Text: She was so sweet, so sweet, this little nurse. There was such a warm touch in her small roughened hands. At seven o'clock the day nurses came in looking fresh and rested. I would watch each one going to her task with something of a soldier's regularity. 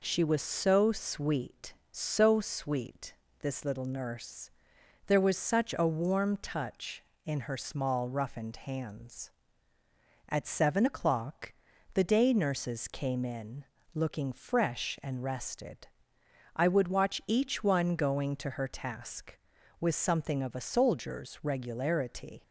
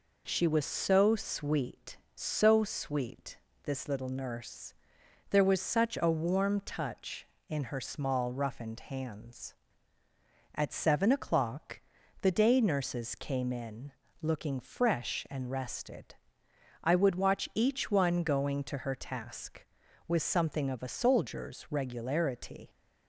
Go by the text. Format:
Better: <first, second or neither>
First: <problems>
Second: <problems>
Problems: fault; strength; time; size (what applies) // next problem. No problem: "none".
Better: neither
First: pauses between "o'clock" and "the"; at 11.5 s; 0.40 s long // pauses between "in" and "looking"; slight; at 13.6 s; 0.30 s long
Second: pauses between "o'clock" and "the"; at 11.8 s; 0.40 s long // pauses between "in" and "looking"; slight; at 13.9 s; 0.30 s long